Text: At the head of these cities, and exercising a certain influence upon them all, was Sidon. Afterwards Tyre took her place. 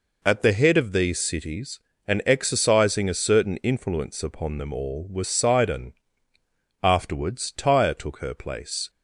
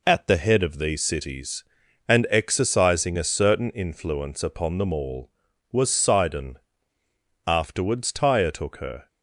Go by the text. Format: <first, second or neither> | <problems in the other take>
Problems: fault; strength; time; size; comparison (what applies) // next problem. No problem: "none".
first | stops before "place"; at 9.0 s